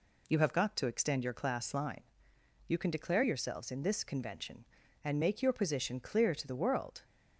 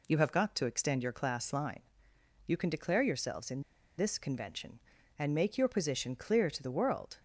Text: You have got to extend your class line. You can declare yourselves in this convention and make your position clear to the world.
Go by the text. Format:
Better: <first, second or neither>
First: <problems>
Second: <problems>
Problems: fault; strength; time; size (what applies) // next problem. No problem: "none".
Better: first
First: none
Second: pauses between "in" and "this"; slight; at 3.6 s; 0.35 s long